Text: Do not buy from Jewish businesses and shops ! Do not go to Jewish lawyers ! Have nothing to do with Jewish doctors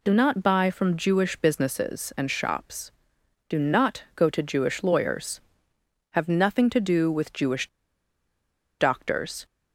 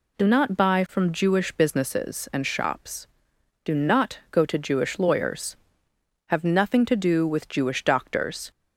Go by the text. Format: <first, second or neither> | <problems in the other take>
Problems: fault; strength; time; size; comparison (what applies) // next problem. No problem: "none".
second | pauses between "Jewish" and "doctors"; at 7.6 s; 1.1 s long